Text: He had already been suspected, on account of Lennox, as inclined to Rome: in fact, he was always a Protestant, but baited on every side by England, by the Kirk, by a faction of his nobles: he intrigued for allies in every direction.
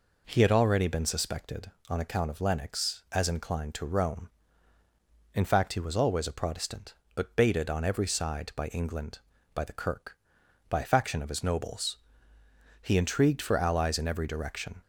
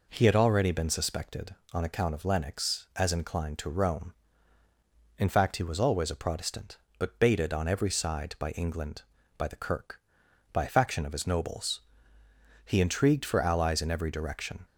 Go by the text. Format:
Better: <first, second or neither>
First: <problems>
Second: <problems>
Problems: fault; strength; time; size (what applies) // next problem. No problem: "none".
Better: neither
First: none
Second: none